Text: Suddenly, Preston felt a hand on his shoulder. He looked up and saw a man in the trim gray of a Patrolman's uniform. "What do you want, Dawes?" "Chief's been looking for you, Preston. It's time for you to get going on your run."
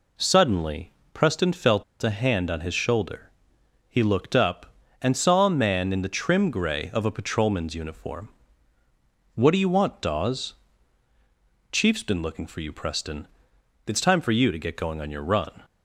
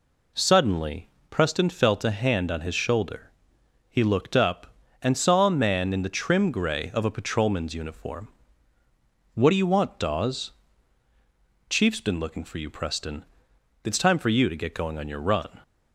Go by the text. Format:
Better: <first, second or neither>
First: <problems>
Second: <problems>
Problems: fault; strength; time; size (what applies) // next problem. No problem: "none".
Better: second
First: pauses between "felt" and "a"; slight; at 1.8 s; 0.18 s long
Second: none